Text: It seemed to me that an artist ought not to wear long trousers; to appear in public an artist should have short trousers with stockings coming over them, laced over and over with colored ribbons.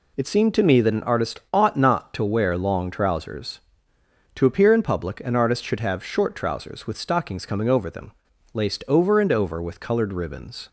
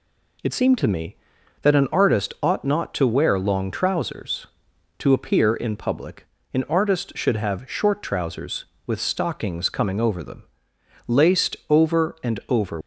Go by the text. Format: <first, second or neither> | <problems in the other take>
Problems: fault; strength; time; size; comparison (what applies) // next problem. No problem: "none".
first | pauses between "public" and "an"; slight; at 6.2 s; 0.27 s long // stops before "with colored ribbons"; at 12.8 s